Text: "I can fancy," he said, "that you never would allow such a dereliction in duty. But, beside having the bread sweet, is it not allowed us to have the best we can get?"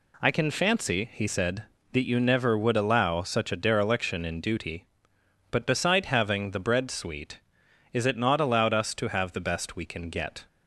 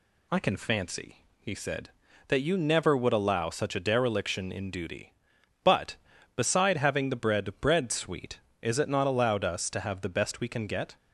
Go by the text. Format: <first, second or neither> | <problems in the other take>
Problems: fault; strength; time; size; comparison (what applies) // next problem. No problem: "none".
first | says "bread" twice; at 7.6 s